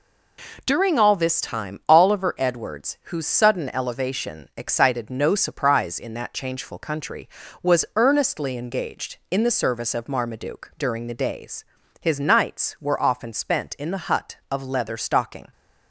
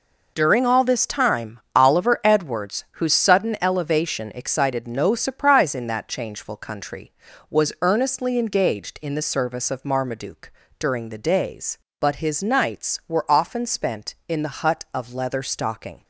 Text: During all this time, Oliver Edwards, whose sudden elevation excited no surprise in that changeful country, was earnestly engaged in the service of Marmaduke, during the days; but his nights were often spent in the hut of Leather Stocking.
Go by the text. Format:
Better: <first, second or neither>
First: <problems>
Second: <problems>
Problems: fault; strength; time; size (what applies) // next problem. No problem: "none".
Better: second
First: skips "but"; at 11.8 s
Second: none